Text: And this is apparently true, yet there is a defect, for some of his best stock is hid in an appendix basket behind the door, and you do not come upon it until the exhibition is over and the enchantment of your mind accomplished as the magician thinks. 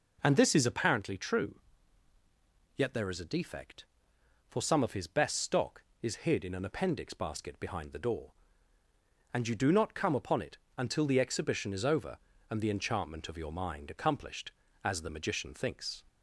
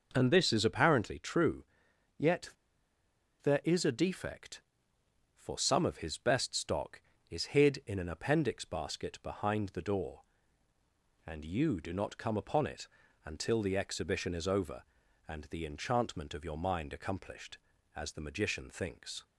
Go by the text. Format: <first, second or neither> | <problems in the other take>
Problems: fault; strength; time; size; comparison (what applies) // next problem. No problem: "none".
first | pauses between "yet" and "there"; noticeable; at 2.5 s; 0.92 s long // pauses between "it" and "until"; at 12.8 s; 0.40 s long; slight in the first